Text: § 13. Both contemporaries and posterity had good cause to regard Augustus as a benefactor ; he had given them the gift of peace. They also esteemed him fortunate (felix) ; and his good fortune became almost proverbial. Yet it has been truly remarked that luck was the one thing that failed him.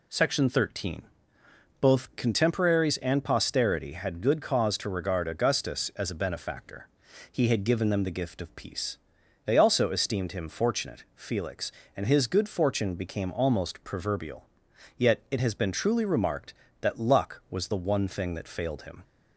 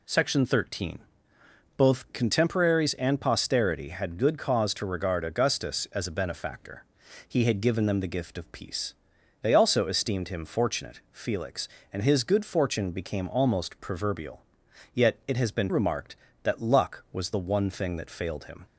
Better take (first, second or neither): first